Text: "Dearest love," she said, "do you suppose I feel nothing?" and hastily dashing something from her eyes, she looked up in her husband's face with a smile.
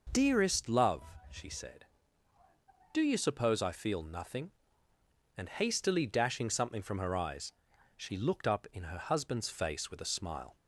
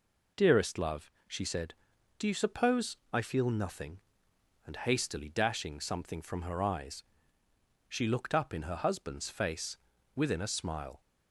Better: first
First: none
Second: says "within" for "with"; at 10.1 s

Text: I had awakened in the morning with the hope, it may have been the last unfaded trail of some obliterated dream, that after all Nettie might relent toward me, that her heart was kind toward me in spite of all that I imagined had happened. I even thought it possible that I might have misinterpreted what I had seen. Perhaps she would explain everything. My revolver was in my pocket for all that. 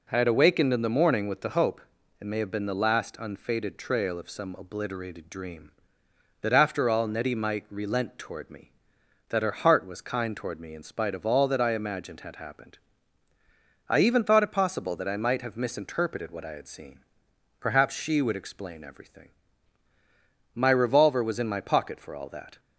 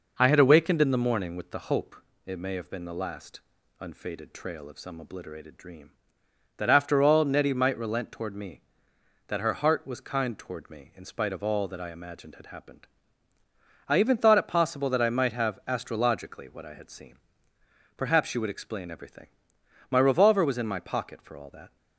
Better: first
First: none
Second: pauses between "last" and "unfaded"; at 3.4 s; 0.40 s long // says "astrologically" for "misinterpreted"; at 15.6 s

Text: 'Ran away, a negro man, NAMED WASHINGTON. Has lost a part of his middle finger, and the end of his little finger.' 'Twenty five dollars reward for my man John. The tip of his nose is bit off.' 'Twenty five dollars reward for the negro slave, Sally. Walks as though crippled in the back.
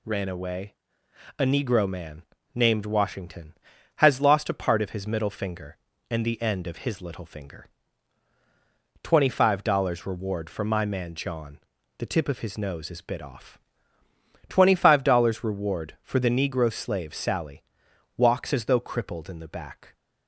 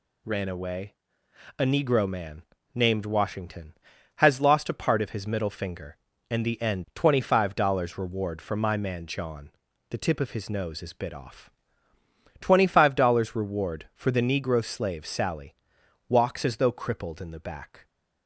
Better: first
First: none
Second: skips "of his little finger"; at 6.8 s

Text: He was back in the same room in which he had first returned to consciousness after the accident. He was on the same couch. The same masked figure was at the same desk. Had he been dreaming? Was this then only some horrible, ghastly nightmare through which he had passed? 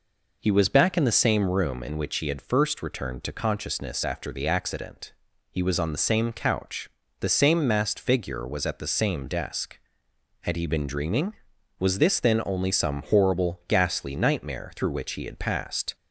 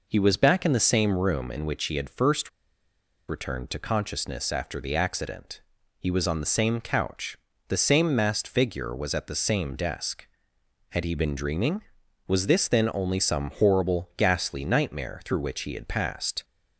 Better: first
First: none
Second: pauses between "first" and "returned"; noticeable; at 2.4 s; 0.78 s long

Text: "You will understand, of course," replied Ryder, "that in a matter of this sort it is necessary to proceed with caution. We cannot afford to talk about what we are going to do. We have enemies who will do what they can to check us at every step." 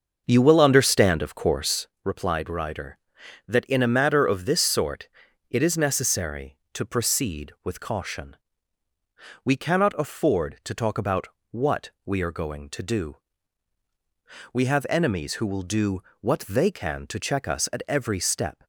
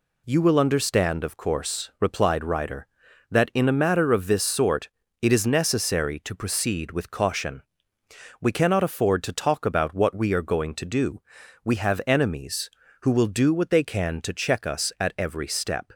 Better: second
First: starts louder than the rest; until 1.8 s; 6.5 dB // pauses between "sort" and "it"; at 5.0 s; 0.41 s long // pauses between "about" and "what"; slight; at 11.2 s; 0.22 s long // pauses between "do" and "what"; slight; at 16.0 s; 0.18 s long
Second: pauses between "sort" and "it"; slight; at 4.8 s; 0.32 s long

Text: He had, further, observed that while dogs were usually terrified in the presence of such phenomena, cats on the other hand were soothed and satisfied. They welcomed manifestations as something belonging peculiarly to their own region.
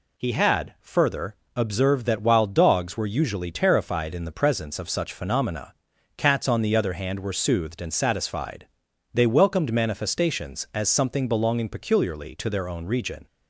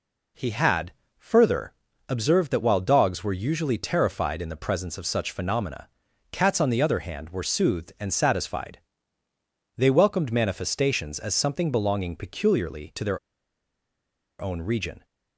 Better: first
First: none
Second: pauses between "their" and "own"; at 13.1 s; 1.2 s long

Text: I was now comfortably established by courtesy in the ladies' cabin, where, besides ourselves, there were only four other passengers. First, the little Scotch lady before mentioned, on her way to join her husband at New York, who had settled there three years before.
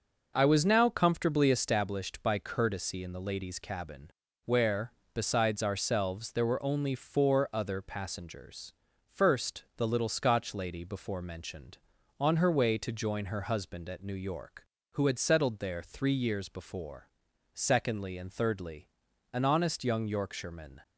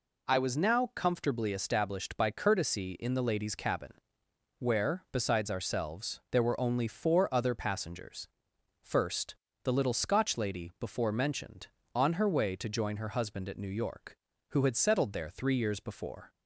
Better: second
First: goes on to say "Secondly and thirdly an honest young Yorkshireman"; strong; from 17.5 s on; 3.2 s long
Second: none

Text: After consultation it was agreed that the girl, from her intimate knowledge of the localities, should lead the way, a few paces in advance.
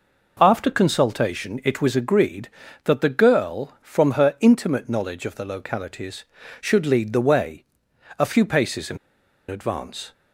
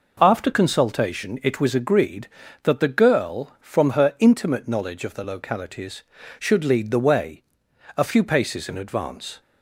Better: second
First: pauses between "in" and "advance"; noticeable; at 8.9 s; 0.52 s long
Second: none

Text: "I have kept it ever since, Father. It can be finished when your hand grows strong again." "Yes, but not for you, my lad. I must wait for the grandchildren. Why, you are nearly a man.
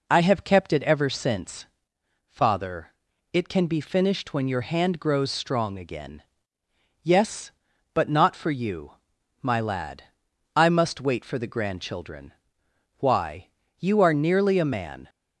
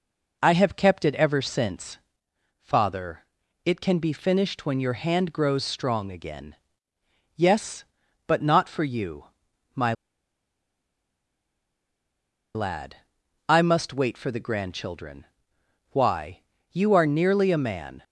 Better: first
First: none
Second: pauses between "my" and "lad"; strong; at 9.9 s; 2.6 s long

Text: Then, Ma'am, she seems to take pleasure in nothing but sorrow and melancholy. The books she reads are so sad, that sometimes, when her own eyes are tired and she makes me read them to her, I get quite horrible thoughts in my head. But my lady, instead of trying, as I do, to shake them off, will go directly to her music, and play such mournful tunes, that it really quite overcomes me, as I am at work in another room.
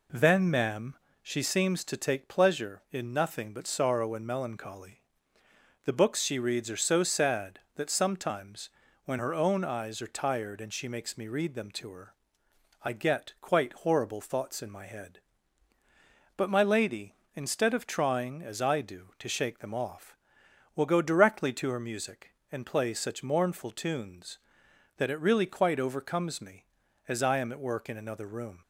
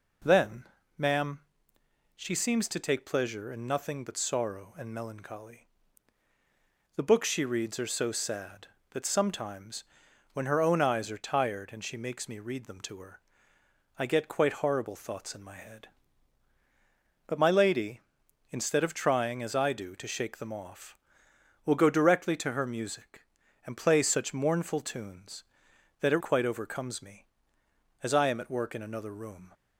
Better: first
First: none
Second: skips "really"; at 26.2 s

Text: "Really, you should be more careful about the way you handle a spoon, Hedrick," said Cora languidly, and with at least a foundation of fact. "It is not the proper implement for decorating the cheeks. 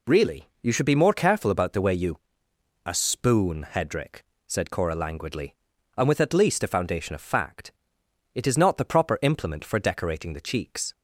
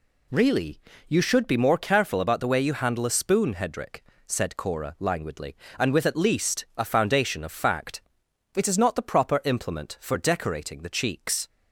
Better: second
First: skips "handle"; at 2.5 s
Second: none

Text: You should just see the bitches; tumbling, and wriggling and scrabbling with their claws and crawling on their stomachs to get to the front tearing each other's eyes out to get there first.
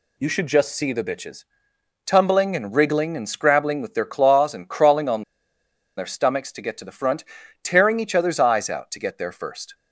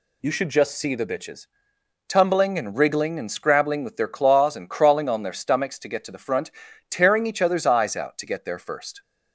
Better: second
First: pauses between "on" and "their"; noticeable; at 5.2 s; 0.74 s long // pauses between "front" and "tearing"; at 7.2 s; 0.38 s long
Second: pauses between "front" and "tearing"; at 6.5 s; 0.38 s long

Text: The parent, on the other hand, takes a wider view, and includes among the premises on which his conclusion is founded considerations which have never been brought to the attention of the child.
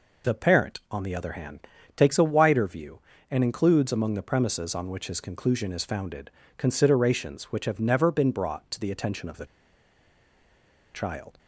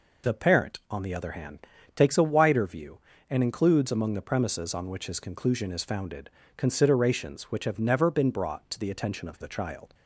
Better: second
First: pauses between "founded" and "considerations"; slight; at 6.3 s; 0.26 s long // pauses between "the" and "child"; strong; at 9.4 s; 1.4 s long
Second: pauses between "founded" and "considerations"; slight; at 6.3 s; 0.26 s long

